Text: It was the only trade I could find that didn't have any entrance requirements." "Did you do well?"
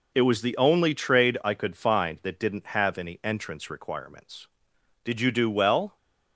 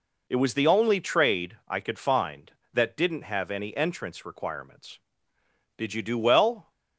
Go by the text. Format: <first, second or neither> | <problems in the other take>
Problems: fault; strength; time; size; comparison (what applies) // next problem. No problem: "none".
neither | none